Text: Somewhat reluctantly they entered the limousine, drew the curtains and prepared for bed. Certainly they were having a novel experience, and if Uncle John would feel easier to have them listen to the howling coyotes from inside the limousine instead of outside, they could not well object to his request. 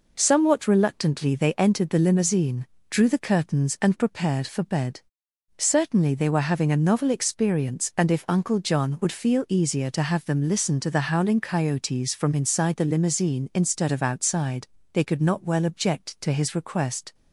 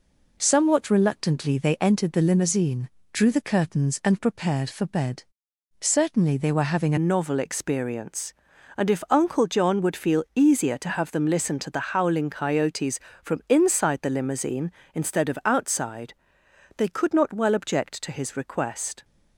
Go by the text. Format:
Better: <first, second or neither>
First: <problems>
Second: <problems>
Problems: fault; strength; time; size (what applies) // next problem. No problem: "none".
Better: first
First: none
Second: changes voice at "novel"; from 6.9 s on; 12.1 s long